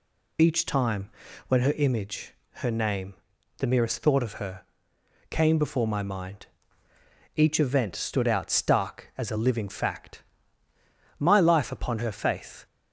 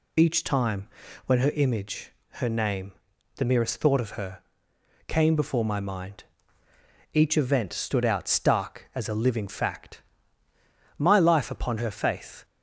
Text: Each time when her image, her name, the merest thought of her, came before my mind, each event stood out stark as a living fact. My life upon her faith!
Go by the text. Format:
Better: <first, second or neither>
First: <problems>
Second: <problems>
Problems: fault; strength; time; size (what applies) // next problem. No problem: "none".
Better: neither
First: pauses between "time" and "when"; at 1.0 s; 0.38 s long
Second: pauses between "time" and "when"; at 0.8 s; 0.38 s long